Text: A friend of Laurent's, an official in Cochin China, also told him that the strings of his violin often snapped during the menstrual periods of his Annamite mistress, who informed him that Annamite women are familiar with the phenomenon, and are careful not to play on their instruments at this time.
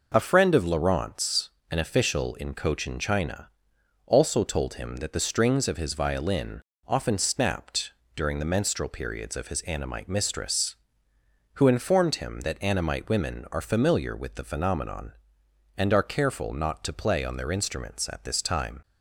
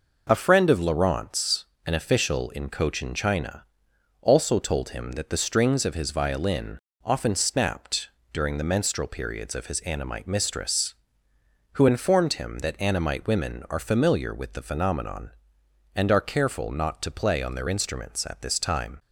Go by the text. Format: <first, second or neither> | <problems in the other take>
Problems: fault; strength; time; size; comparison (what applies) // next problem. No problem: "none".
neither | pauses between "violin" and "often"; slight; the same in both // pauses between "snapped" and "during"; slight; the same in both